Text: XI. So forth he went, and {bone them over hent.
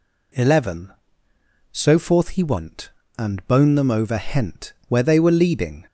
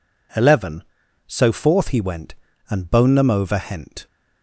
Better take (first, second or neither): second